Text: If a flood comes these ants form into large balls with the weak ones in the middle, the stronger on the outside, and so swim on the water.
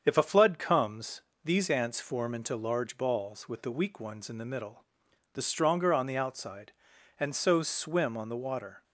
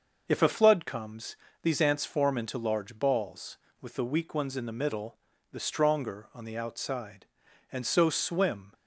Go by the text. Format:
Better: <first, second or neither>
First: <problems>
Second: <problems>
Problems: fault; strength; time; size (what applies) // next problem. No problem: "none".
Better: first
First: starts louder than the rest; strong; until 1.0 s; 7.5 dB // pauses between "comes" and "these"; slight; at 1.2 s; 0.22 s long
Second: starts louder than the rest; noticeable; until 1.2 s; 6 dB // pauses between "comes" and "these"; slight; at 1.3 s; 0.28 s long // stops before "on the water"; at 8.7 s